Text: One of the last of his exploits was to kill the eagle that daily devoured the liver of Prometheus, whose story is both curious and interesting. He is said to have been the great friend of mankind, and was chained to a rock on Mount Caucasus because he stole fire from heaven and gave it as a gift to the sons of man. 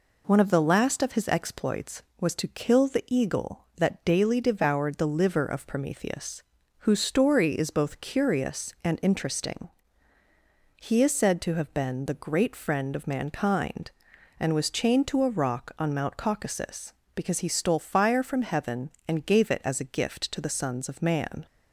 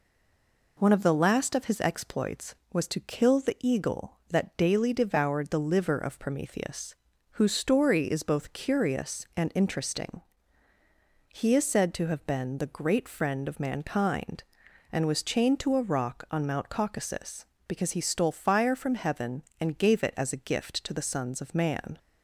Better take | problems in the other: first | stays silent before the first word; slight; until 0.7 s; 0.7 s long

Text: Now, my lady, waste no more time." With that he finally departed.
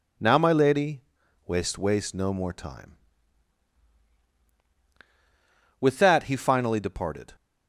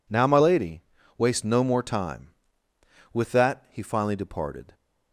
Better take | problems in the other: second | says "waste" twice; at 1.7 s

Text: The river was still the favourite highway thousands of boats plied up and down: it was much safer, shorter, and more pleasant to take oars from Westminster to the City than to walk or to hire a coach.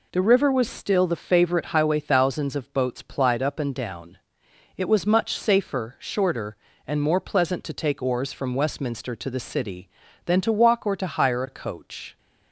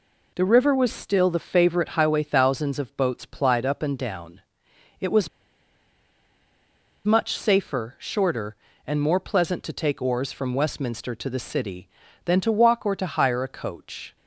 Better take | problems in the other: first | pauses between "was" and "much"; strong; at 5.2 s; 1.7 s long

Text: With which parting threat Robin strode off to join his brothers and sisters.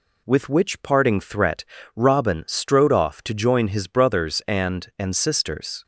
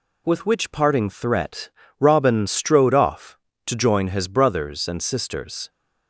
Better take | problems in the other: second | pauses between "threat" and "Robin"; slight; at 1.6 s; 0.32 s long; slight in the second // says "and" twice; at 4.9 s

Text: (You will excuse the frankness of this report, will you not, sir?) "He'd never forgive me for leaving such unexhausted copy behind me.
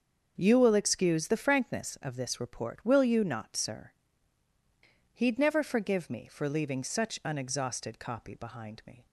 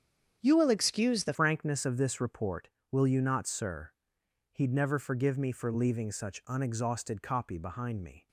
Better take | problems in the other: first | starts louder than the rest; strong; until 1.4 s; 8 dB; also in the first // changes voice at "frankness"; from 1.3 s on; 6.9 s long

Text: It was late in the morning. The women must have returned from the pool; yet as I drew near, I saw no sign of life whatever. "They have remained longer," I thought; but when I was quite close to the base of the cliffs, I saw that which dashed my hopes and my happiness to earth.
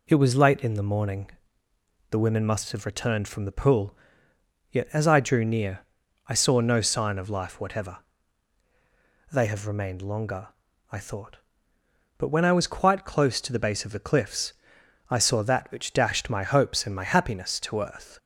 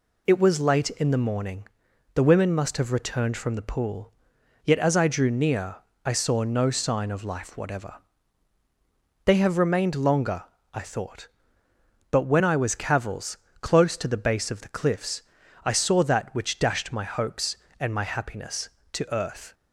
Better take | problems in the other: first | says "cavils" for "quite"; at 12.7 s

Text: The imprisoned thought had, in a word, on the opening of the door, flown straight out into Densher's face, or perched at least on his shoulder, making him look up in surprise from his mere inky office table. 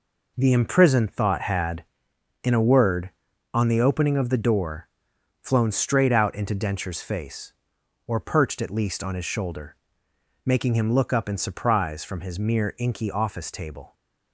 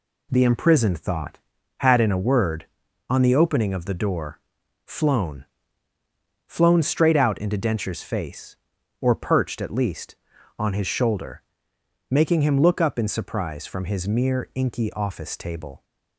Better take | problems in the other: first | says "flown" twice; at 6.4 s

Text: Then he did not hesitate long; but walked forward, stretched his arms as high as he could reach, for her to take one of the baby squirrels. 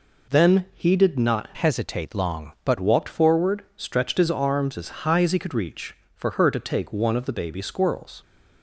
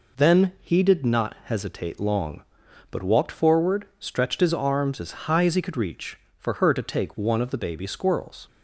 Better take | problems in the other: second | changes voice from "hesitate" to "but"; from 1.5 to 2.7 s; 1.2 s long

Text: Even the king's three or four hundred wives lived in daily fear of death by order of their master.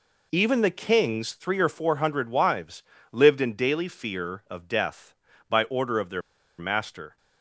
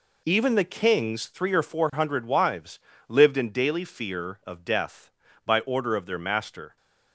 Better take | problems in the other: second | pauses between "wives" and "lived"; slight; at 2.8 s; 0.28 s long; slight in the second // pauses between "their" and "master"; at 6.2 s; 0.37 s long

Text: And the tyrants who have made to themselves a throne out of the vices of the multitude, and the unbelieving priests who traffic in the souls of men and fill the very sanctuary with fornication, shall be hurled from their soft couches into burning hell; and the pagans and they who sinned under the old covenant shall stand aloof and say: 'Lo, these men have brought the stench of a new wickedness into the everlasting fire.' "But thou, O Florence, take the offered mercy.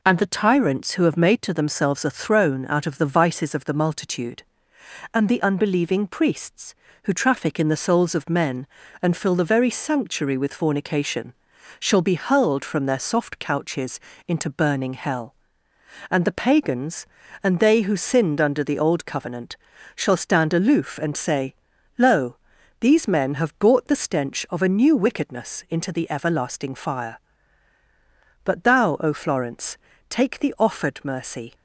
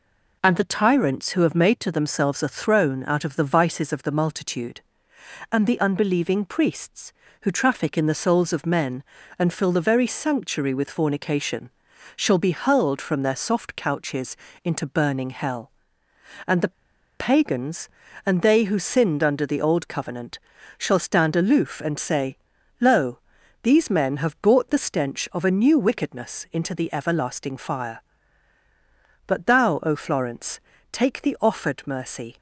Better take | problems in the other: first | pauses between "couches" and "into"; slight; at 14.3 s; 0.26 s long; slight in the first // pauses between "the" and "pagans"; noticeable; at 16.7 s; 0.48 s long // pauses between "covenant" and "shall"; at 20.3 s; 0.40 s long; also in the first

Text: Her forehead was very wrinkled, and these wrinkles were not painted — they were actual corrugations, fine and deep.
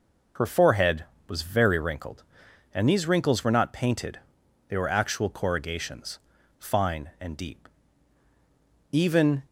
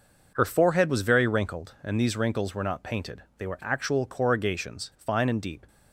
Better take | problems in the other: second | goes on to say "Even"; from 8.9 s on; 0.52 s long

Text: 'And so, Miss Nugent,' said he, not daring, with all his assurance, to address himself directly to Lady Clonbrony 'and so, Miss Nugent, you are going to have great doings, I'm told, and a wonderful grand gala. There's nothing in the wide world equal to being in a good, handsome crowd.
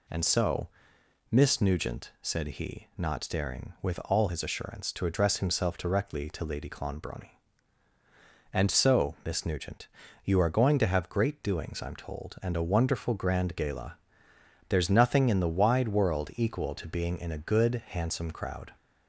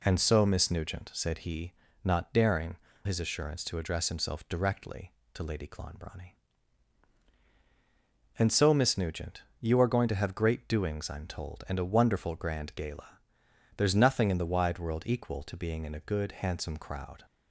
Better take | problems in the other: first | skips "with all"; at 2.9 s

